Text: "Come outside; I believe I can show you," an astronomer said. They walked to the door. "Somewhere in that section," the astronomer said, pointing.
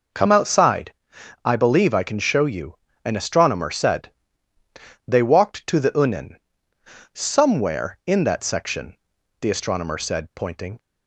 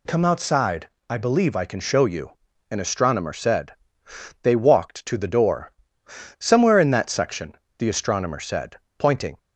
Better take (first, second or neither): second